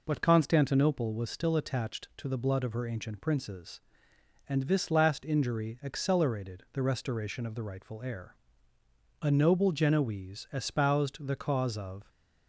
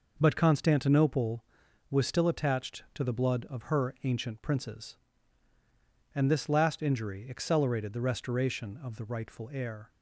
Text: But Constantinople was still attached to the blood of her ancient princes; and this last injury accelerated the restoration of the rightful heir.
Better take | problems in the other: second | goes on to say "A noble Genoese espoused the cause of"; strong; from 9.2 s on; 2.8 s long

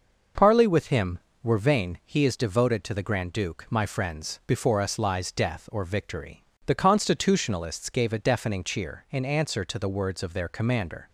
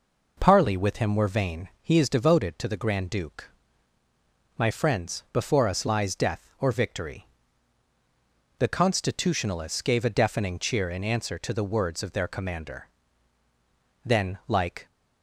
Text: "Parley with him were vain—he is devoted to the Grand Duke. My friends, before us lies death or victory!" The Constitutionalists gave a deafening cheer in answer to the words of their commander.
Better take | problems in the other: first | goes on to say "Then like"; noticeable; from 14.0 s on; 0.82 s long

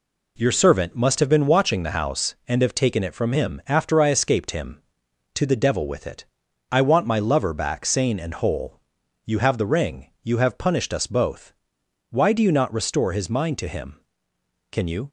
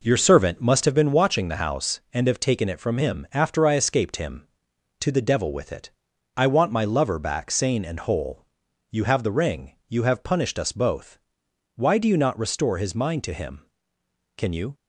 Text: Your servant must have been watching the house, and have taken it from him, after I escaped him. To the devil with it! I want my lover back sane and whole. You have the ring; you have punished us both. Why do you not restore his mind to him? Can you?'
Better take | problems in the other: first | starts louder than the rest; noticeable; until 0.9 s; 4.5 dB

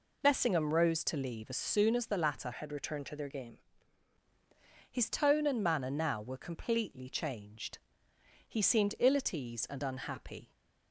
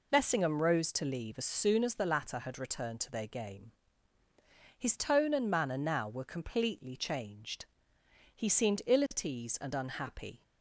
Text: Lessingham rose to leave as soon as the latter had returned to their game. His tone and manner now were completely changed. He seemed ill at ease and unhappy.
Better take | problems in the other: second | changes voice from "had" to "game"; from 2.5 to 3.5 s; 1.0 s long

